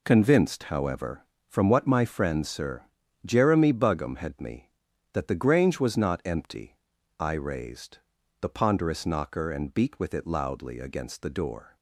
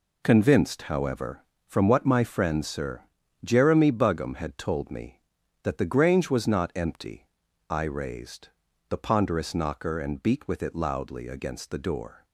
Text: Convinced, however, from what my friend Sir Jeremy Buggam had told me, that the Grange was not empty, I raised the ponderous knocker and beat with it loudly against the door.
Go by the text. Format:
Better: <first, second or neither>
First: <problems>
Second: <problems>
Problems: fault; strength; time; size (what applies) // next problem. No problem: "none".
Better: second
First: pauses between "Sir" and "Jeremy"; at 2.8 s; 0.42 s long // skips "told"; at 4.3 s // pauses between "raised" and "the"; at 7.9 s; 0.42 s long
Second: pauses between "Sir" and "Jeremy"; at 3.0 s; 0.42 s long // pauses between "raised" and "the"; at 8.4 s; 0.40 s long